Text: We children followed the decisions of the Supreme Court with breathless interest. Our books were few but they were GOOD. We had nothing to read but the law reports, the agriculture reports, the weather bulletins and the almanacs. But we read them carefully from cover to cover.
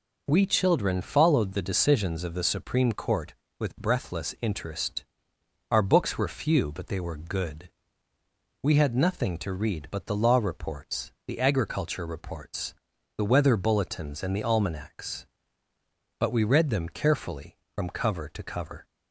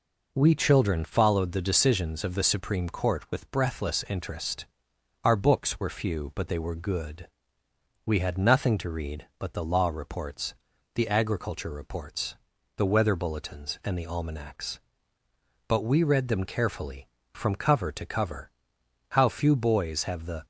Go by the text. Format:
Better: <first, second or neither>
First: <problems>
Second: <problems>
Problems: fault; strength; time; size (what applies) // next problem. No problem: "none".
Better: first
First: none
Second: goes on to say "How few boys have the"; from 19.1 s on; 1.3 s long